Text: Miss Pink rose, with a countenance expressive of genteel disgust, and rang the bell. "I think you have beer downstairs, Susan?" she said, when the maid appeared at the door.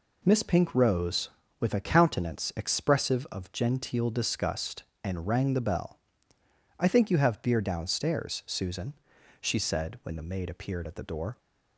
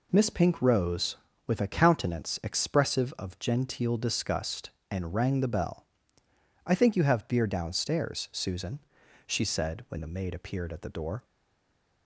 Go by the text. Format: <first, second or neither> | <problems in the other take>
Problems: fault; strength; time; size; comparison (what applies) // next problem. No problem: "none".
first | stays silent after the last word; slight; from 11.2 s on; 0.8 s long